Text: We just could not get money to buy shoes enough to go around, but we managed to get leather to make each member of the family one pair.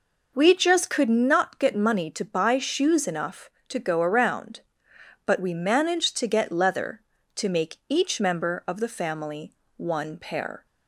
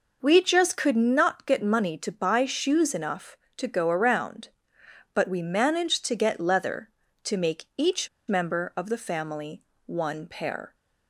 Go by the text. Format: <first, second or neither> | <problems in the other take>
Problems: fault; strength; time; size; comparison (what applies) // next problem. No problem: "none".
first | pauses between "each" and "member"; slight; at 8.0 s; 0.19 s long // pauses between "family" and "one"; slight; at 9.6 s; 0.22 s long; slight in the first